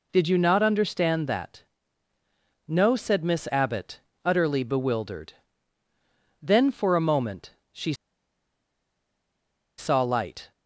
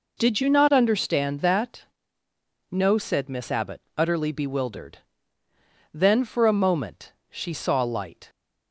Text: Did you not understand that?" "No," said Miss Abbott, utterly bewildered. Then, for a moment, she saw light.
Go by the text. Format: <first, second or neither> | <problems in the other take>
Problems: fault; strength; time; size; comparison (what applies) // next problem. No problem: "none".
second | pauses between "she" and "saw"; strong; at 7.9 s; 1.8 s long